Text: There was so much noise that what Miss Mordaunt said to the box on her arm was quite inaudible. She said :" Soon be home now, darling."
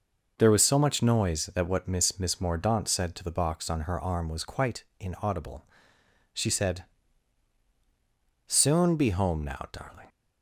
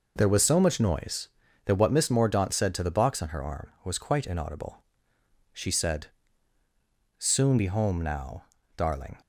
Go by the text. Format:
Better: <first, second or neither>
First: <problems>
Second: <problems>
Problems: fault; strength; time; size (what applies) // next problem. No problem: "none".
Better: second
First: starts louder than the rest; until 1.3 s; 6.5 dB // says "Miss" twice; at 2.1 s // pauses between "quite" and "inaudible"; slight; at 4.8 s; 0.16 s long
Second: none